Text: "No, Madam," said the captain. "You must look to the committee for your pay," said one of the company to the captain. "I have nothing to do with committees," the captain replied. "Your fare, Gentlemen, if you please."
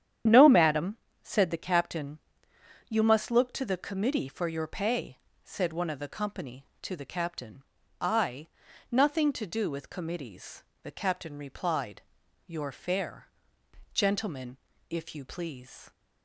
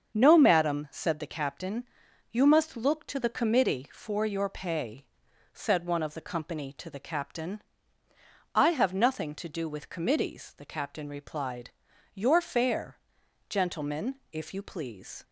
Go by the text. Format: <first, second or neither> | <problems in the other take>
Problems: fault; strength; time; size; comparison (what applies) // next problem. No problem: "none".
second | starts louder than the rest; strong; until 1.5 s; 9.5 dB; also in the second // skips "have"; at 8.6 s